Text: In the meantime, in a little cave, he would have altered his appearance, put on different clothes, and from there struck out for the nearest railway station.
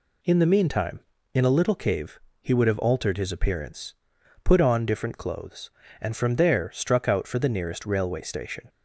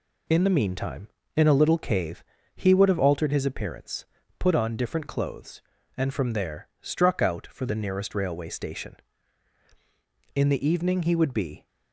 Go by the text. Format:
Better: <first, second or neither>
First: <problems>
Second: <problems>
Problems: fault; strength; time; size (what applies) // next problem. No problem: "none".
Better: first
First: none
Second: goes on to say "In the evening he would be"; from 10.3 s on; 1.3 s long